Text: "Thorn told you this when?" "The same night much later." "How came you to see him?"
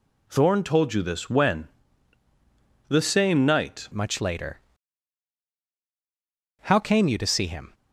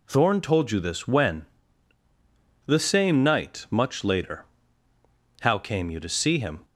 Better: second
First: changes voice at "much"; from 3.9 s on; 3.8 s long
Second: none

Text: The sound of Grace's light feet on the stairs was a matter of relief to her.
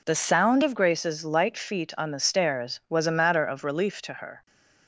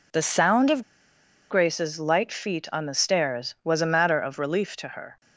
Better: first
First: none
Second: pauses between "of" and "Grace's"; noticeable; at 0.8 s; 0.67 s long

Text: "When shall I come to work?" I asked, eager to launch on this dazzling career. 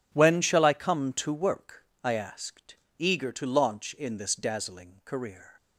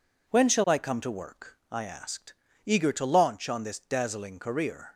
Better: second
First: says "in" for "on"; at 3.9 s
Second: none

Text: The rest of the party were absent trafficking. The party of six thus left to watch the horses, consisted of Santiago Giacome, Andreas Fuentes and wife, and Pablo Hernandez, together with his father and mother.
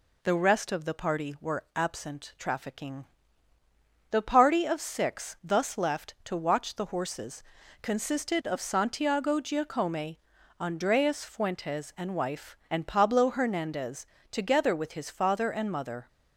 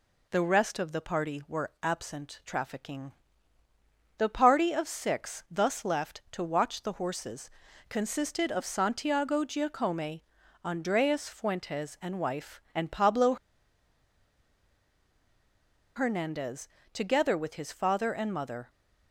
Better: first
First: none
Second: pauses between "Pablo" and "Hernandez"; strong; at 13.3 s; 2.6 s long

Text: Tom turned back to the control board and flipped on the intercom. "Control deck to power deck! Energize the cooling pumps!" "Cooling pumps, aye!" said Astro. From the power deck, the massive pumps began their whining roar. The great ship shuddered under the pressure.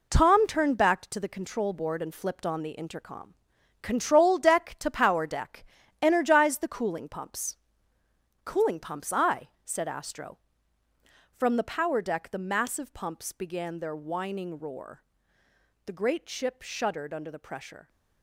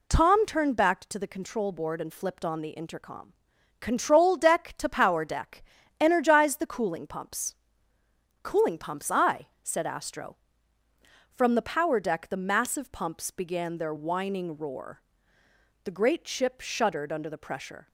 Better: second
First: gets quieter; strong; throughout; 8 dB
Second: none

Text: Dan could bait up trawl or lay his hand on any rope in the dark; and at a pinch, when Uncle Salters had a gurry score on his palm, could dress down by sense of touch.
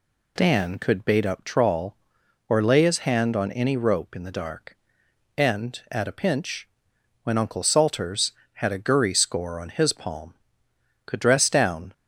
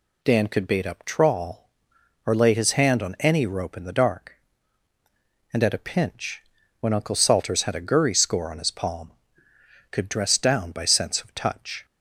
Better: second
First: stops before "by sense of touch"; at 11.9 s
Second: none

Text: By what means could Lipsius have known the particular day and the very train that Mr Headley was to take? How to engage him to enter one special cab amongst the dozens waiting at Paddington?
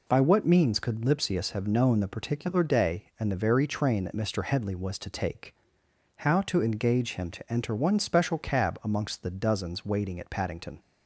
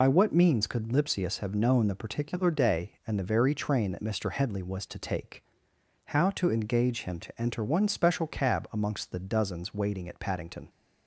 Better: first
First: none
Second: loses the start of "By"; at 0.0 s; 45 ms

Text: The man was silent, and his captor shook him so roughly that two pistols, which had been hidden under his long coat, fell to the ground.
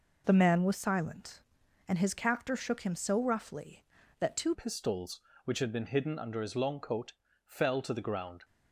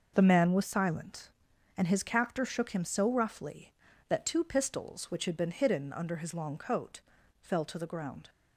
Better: second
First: changes voice at "pistols"; from 4.5 s on; 3.9 s long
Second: none

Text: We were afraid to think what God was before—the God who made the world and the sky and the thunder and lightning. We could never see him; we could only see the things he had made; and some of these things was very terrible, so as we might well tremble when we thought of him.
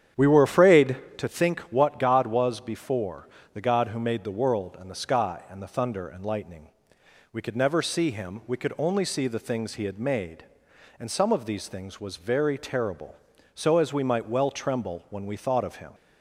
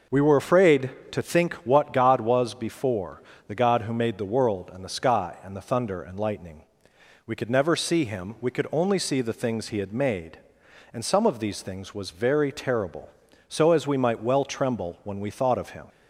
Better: second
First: starts louder than the rest; strong; until 1.2 s; 9.5 dB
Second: none

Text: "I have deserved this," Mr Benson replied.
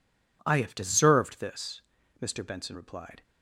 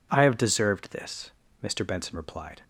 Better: neither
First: none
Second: none

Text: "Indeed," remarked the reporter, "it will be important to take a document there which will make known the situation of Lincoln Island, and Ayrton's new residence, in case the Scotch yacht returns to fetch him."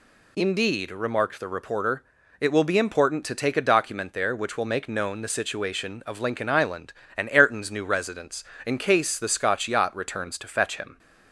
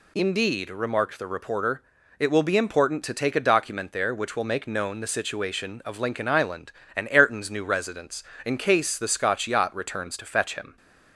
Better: neither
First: none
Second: none

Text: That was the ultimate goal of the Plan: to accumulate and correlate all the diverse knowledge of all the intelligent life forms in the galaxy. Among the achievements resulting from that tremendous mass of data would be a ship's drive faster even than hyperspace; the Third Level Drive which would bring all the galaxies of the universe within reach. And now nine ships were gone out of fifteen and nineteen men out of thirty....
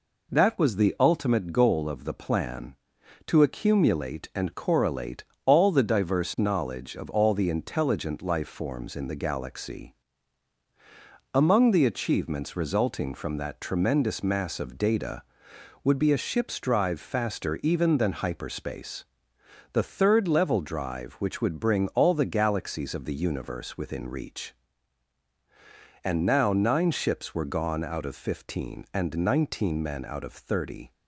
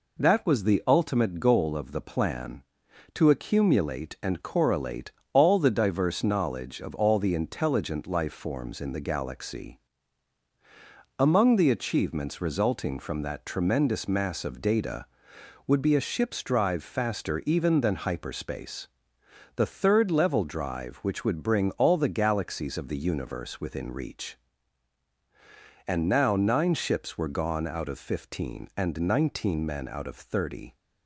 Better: neither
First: pauses between "correlate" and "all"; slight; at 5.2 s; 0.24 s long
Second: pauses between "correlate" and "all"; slight; at 5.1 s; 0.24 s long

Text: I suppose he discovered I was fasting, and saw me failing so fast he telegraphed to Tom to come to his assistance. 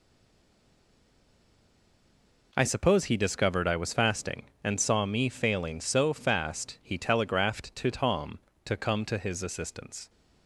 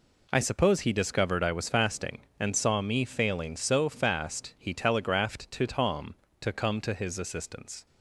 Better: second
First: stays silent before the first word; strong; until 2.5 s; 2.5 s long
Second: none

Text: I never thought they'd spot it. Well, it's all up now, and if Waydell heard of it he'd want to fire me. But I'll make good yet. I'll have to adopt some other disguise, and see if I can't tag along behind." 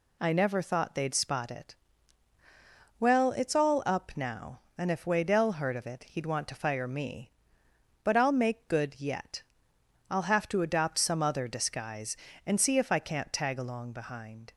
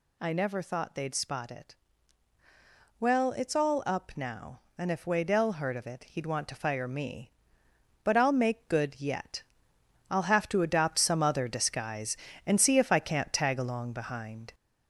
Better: first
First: none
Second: gets louder; throughout; 3.5 dB

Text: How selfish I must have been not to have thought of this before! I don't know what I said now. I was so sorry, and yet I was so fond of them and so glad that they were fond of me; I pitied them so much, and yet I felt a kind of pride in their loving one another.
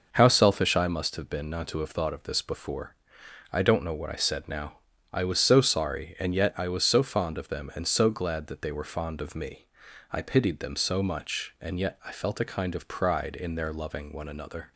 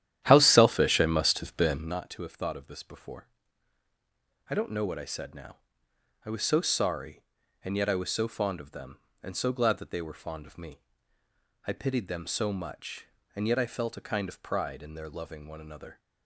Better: first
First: none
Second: starts louder than the rest; strong; until 2.0 s; 11 dB

